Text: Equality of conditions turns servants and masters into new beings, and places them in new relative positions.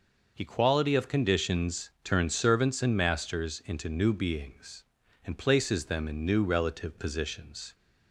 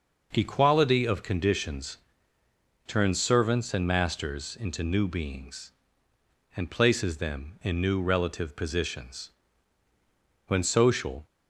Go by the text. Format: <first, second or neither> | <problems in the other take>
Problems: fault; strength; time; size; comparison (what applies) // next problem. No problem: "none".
first | pauses between "conditions" and "turns"; noticeable; at 1.9 s; 0.90 s long // goes on to say "When social"; noticeable; from 10.4 s on; 0.78 s long